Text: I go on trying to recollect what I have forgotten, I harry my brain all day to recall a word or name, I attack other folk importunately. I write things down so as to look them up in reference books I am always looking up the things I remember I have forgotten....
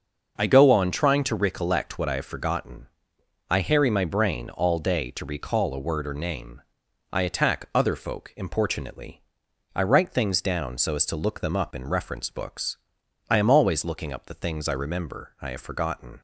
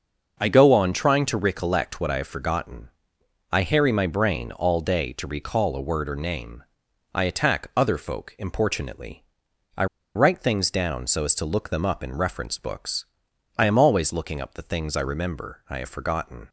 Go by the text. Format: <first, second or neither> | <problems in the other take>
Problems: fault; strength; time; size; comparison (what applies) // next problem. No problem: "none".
first | starts louder than the rest; until 1.4 s; 6 dB; also in the first // pauses between "I" and "write"; slight; at 9.8 s; 0.30 s long // pauses between "books" and "I"; noticeable; at 13.0 s; 0.54 s long; noticeable in the first